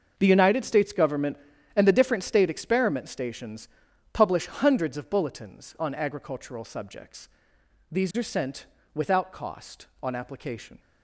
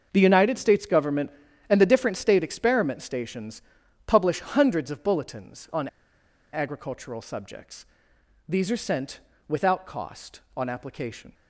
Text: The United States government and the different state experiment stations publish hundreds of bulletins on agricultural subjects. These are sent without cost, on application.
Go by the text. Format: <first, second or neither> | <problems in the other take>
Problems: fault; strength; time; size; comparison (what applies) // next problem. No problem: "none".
first | starts louder than the rest; until 1.1 s; 6.5 dB; also in the first // pauses between "stations" and "publish"; noticeable; at 3.6 s; 0.46 s long; noticeable in the first // pauses between "on" and "agricultural"; noticeable; at 5.8 s; 0.65 s long // pauses between "sent" and "without"; slight; at 9.1 s; 0.28 s long; slight in the first